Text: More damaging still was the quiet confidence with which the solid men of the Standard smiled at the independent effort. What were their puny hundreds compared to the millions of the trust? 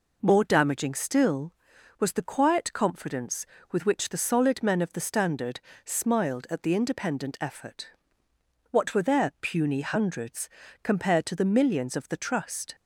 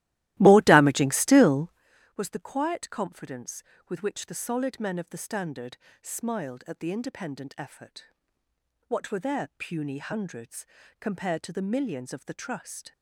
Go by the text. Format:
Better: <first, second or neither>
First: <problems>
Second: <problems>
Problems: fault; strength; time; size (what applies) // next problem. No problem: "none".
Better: first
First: pauses between "Standard" and "smiled"; slight; at 5.6 s; 0.24 s long // pauses between "hundreds" and "compared"; slight; at 10.4 s; 0.34 s long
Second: starts louder than the rest; strong; until 1.9 s; 16 dB // pauses between "Standard" and "smiled"; slight; at 5.7 s; 0.24 s long // pauses between "hundreds" and "compared"; slight; at 10.6 s; 0.34 s long